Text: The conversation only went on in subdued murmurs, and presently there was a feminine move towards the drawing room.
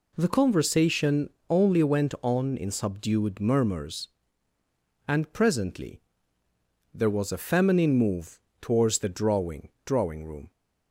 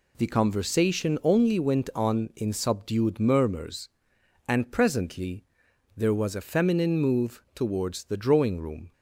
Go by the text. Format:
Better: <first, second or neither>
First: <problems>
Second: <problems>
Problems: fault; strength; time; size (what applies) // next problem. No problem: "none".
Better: second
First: pauses between "conversation" and "only"; slight; at 1.3 s; 0.18 s long // pauses between "presently" and "there"; noticeable; at 6.0 s; 0.92 s long // pauses between "move" and "towards"; slight; at 8.3 s; 0.22 s long // says "drawing" twice; at 9.8 s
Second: pauses between "presently" and "there"; noticeable; at 5.4 s; 0.50 s long